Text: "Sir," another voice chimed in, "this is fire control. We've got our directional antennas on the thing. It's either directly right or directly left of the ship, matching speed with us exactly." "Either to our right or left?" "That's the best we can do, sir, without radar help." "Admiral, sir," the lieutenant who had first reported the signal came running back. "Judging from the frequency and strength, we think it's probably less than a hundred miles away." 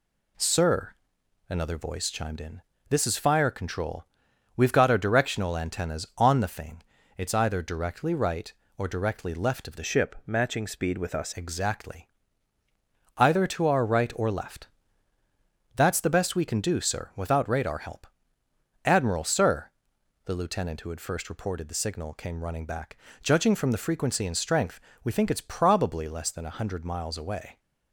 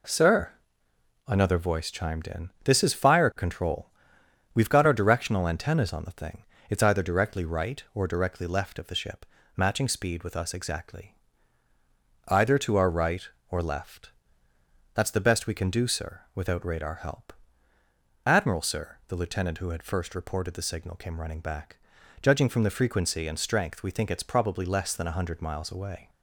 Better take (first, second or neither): second